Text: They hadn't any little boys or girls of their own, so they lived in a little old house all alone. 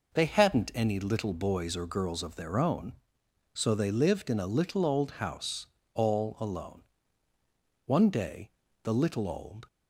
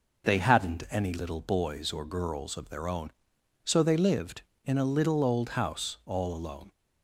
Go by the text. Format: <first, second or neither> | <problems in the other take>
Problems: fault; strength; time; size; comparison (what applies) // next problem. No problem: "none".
second | pauses between "house" and "all"; slight; at 5.6 s; 0.28 s long // goes on to say "One day the little old"; strong; from 7.8 s on; 1.8 s long